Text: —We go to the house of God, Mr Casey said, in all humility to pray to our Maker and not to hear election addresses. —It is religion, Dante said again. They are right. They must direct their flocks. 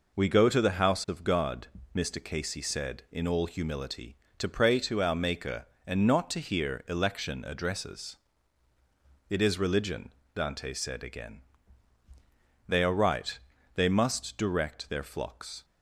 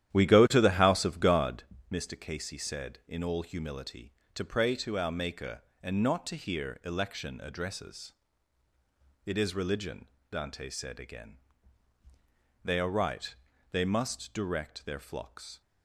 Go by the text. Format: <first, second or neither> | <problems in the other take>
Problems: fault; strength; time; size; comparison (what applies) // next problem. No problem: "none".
first | starts louder than the rest; strong; until 1.7 s; 11.5 dB